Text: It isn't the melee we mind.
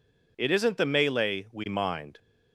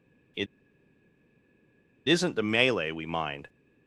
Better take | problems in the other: first | pauses between "It" and "isn't"; strong; at 0.4 s; 1.6 s long

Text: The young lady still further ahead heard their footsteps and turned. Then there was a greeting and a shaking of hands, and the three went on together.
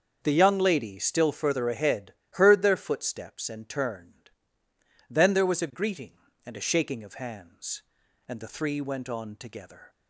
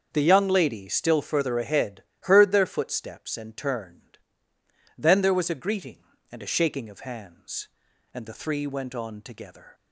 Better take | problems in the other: neither | starts louder than the rest; the same in both // pauses between "ahead" and "heard"; slight; the same in both

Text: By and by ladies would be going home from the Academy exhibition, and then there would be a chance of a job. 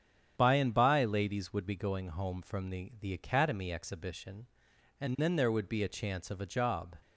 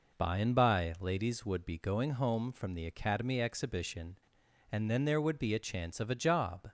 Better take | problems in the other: second | starts louder than the rest; strong; until 1.3 s; 9 dB // says "the" twice; at 3.0 s

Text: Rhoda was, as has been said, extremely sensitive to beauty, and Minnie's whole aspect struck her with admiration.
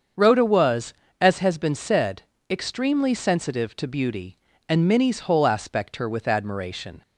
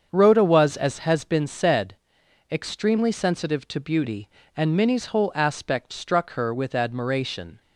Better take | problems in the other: second | starts louder than the rest; until 1.4 s; 7 dB; also in the second // skips "struck"; at 5.9 s

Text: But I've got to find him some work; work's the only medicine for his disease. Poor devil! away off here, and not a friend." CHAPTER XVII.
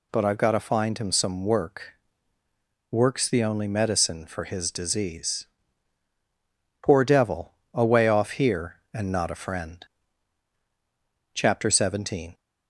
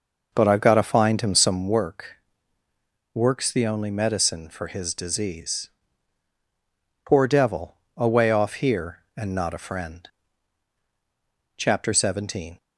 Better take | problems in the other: first | starts louder than the rest; noticeable; until 1.8 s; 5.5 dB

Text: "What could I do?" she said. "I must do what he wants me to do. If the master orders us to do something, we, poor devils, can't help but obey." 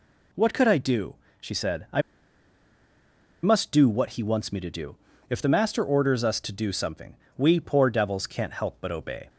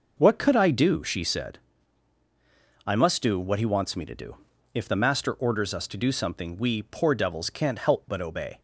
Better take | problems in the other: second | pauses between "I" and "must"; strong; at 2.0 s; 1.4 s long

